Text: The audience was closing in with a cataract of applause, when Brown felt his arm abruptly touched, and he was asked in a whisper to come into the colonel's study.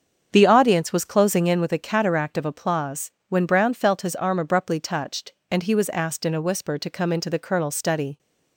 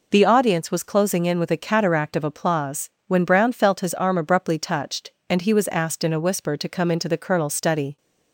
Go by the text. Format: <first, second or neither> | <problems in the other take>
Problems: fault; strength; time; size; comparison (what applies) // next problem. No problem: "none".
second | starts louder than the rest; until 1.7 s; 7 dB